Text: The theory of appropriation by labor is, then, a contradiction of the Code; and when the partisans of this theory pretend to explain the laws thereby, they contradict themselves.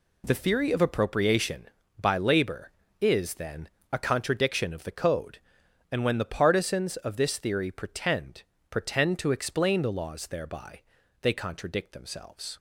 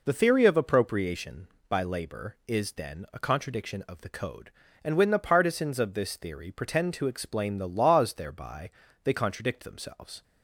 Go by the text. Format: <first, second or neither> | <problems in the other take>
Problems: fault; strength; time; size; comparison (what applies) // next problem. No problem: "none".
second | says "pretend" twice; at 8.7 s